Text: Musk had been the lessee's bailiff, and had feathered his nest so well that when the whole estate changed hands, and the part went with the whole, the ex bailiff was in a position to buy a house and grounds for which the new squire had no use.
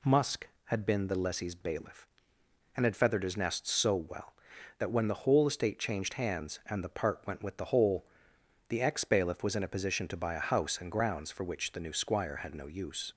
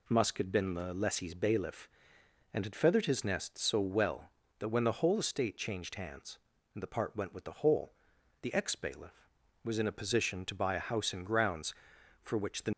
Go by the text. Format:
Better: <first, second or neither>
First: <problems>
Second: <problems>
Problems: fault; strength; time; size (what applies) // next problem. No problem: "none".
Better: first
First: none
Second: stops before "new squire had no use"; at 12.7 s